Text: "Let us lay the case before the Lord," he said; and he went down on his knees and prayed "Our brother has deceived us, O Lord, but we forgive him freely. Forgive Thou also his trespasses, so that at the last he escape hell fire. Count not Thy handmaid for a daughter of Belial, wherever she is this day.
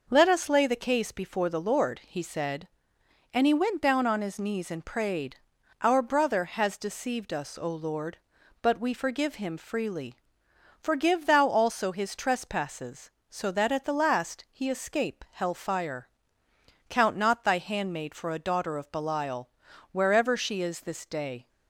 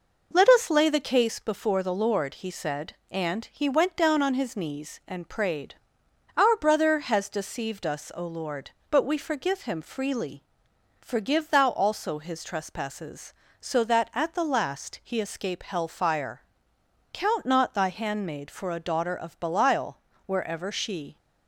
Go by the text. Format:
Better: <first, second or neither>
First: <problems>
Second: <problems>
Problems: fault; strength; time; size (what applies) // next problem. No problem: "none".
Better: first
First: pauses between "prayed" and "Our"; noticeable; at 5.3 s; 0.46 s long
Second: pauses between "prayed" and "Our"; noticeable; at 5.7 s; 0.64 s long // stops before "is this day"; at 21.1 s